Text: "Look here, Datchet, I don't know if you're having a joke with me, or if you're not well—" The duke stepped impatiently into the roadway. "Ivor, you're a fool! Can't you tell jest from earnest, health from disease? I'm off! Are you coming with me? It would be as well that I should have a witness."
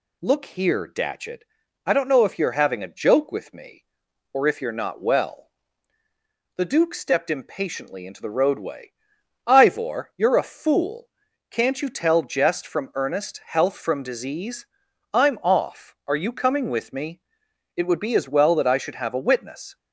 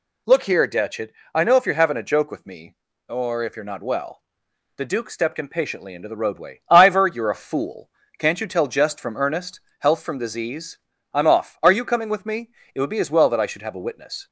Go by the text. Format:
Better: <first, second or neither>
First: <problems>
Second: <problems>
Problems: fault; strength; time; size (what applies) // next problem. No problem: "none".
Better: first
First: none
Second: skips "don't"; at 1.4 s